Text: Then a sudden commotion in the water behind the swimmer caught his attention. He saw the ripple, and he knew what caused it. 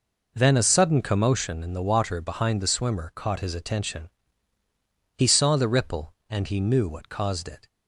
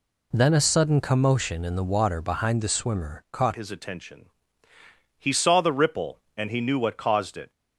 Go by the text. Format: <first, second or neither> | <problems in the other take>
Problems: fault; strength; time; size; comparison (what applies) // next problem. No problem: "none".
first | changes voice at "his"; from 3.5 s on; 4.0 s long